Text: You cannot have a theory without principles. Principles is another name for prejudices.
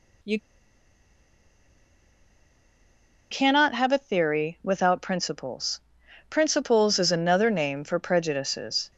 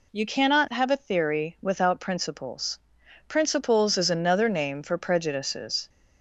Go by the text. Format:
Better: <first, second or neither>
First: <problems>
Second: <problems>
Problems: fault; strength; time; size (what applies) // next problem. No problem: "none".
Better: second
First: pauses between "You" and "cannot"; strong; at 0.3 s; 2.9 s long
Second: none